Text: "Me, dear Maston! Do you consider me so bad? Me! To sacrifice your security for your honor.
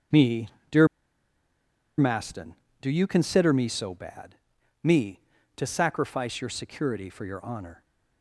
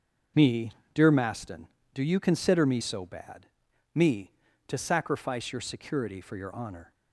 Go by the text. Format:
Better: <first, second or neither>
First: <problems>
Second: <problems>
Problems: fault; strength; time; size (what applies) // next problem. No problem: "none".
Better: second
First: starts louder than the rest; until 2.4 s; 6.5 dB // pauses between "dear" and "Maston"; at 0.8 s; 1.1 s long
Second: starts louder than the rest; until 1.5 s; 6.5 dB